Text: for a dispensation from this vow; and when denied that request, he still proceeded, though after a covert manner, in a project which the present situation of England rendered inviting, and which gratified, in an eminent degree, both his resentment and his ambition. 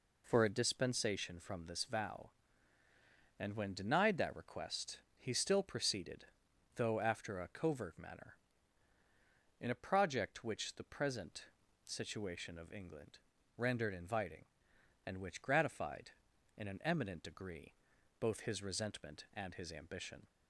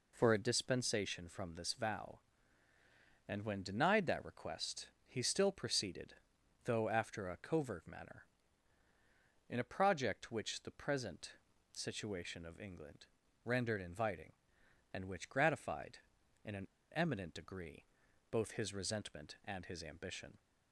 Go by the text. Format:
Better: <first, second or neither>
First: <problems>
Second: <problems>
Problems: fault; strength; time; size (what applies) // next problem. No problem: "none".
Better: first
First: pauses between "present" and "situation"; at 11.4 s; 0.40 s long // pauses between "England" and "rendered"; at 13.1 s; 0.38 s long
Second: pauses between "present" and "situation"; at 11.3 s; 0.40 s long // pauses between "England" and "rendered"; at 13.0 s; 0.38 s long // pauses between "an" and "eminent"; slight; at 16.6 s; 0.26 s long